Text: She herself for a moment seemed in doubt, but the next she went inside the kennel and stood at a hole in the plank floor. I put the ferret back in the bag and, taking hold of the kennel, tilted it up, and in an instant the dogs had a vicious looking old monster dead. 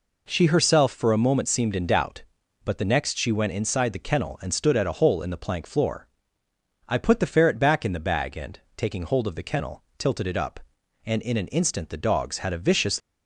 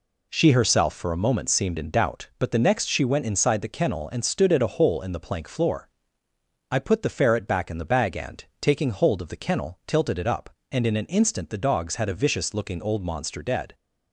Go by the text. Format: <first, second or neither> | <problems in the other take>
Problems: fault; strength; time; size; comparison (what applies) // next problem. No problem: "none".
second | stops before "looking old monster dead"; at 12.9 s